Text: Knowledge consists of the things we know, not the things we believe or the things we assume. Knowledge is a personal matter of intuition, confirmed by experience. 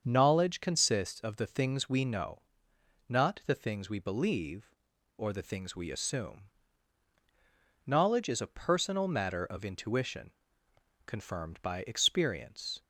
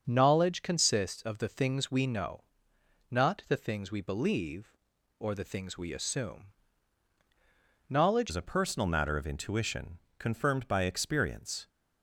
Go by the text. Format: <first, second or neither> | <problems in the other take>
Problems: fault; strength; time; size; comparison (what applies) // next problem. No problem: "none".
first | starts louder than the rest; until 1.0 s; 6.5 dB; strong in the first // changes voice at "is"; from 8.2 s on; 3.4 s long